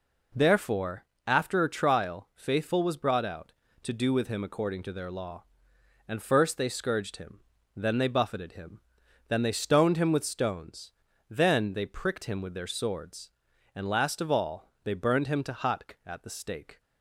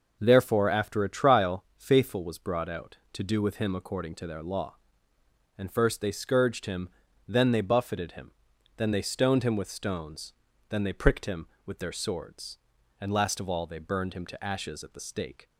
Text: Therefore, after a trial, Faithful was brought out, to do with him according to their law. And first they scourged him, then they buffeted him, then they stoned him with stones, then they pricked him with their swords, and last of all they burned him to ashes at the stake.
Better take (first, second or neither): second